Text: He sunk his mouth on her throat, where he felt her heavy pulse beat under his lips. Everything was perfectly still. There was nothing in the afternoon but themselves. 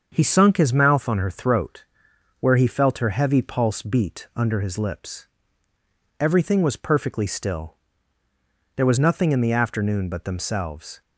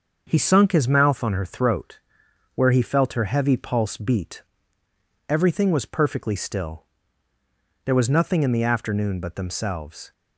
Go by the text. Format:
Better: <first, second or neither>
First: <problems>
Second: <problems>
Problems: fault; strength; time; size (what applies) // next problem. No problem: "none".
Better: first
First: starts louder than the rest; until 1.1 s; 7 dB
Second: starts louder than the rest; until 1.2 s; 6.5 dB // skips "under his lips"; at 4.8 s